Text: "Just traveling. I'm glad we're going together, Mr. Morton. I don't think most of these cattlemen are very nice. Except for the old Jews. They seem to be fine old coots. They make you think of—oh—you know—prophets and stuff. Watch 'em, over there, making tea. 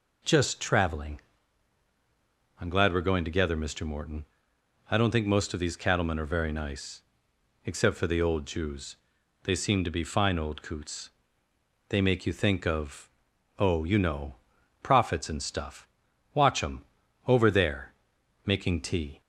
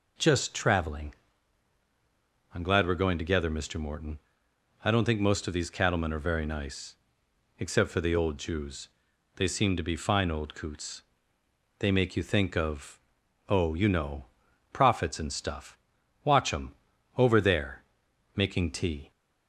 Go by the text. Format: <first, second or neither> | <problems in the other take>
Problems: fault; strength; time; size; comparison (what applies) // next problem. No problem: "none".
neither | none